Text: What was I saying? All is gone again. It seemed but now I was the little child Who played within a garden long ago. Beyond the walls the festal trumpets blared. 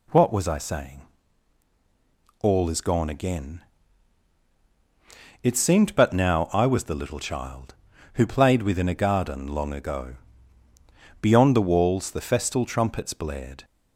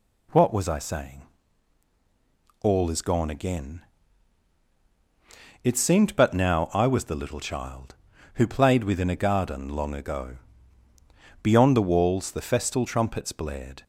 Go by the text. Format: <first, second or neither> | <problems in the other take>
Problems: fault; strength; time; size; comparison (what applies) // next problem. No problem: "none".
neither | none